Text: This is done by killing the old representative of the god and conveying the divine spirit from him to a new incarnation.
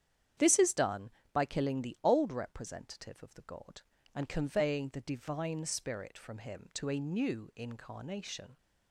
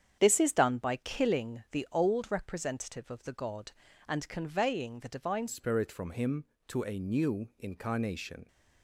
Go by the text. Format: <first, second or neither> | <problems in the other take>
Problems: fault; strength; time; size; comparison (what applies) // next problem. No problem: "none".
first | starts louder than the rest; strong; until 1.2 s; 8.5 dB; strong in the first // changes voice at "spirit"; from 5.4 s on; 3.0 s long